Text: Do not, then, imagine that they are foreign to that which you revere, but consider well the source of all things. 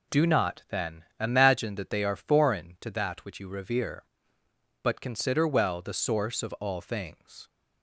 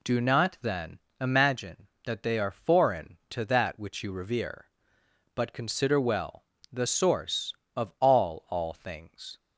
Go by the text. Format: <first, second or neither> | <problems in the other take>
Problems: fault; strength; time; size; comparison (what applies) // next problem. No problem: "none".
first | pauses between "well" and "the"; slight; at 6.4 s; 0.28 s long // says "all" twice; at 8.4 s